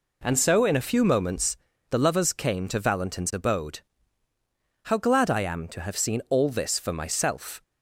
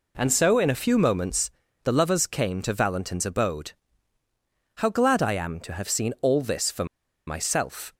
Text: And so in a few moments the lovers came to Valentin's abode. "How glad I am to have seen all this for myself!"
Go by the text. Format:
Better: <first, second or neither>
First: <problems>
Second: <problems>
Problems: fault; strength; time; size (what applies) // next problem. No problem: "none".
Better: first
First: pauses between "moments" and "the"; slight; at 1.5 s; 0.34 s long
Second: pauses between "moments" and "the"; slight; at 1.4 s; 0.34 s long // pauses between "for" and "myself"; at 6.8 s; 0.41 s long